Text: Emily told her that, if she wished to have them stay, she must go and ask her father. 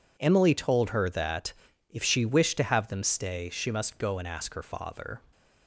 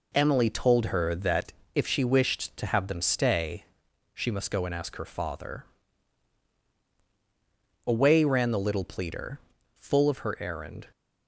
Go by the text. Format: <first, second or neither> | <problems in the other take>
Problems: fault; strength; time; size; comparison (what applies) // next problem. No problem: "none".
first | goes on to say "Away ran the little pleader full of her errand"; strong; from 7.8 s on; 3.0 s long